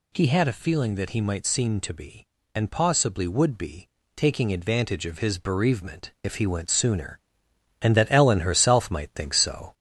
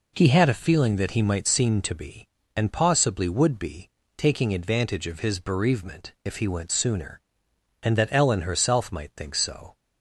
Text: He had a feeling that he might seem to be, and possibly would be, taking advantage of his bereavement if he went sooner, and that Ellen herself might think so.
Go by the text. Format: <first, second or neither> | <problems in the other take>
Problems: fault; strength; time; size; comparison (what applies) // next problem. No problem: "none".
second | gets louder; throughout; 3.5 dB